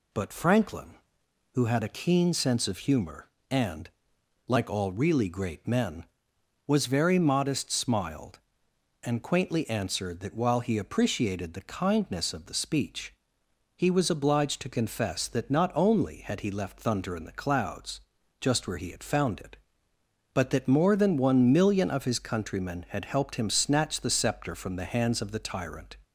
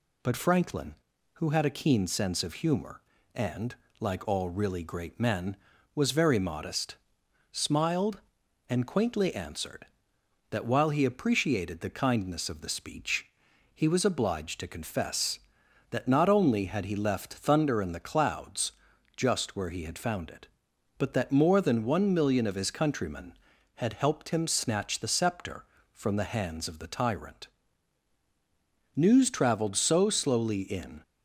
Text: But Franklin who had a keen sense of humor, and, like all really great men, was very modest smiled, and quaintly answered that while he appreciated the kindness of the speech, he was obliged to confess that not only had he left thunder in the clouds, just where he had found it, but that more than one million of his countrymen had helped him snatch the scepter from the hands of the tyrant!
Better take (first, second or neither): first